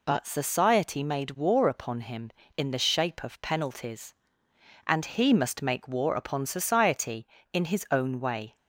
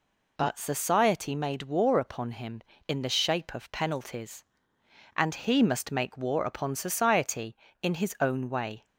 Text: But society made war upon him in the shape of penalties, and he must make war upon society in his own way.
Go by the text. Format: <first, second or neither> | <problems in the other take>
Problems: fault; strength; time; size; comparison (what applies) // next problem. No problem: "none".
neither | none